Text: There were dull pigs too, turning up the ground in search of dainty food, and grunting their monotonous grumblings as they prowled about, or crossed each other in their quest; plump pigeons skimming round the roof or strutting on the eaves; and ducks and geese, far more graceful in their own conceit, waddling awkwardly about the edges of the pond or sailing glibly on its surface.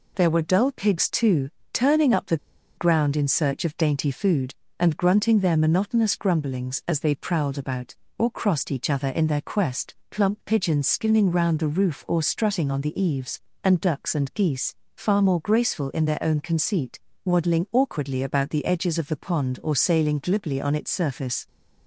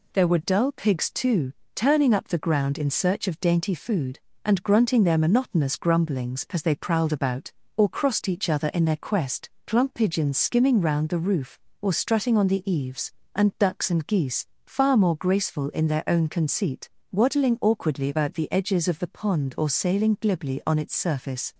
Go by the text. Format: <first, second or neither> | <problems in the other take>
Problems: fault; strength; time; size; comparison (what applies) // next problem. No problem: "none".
second | pauses between "the" and "ground"; at 2.3 s; 0.41 s long